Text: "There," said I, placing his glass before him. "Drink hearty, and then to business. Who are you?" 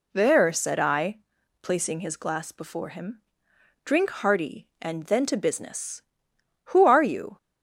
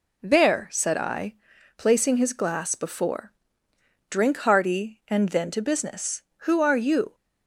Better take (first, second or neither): first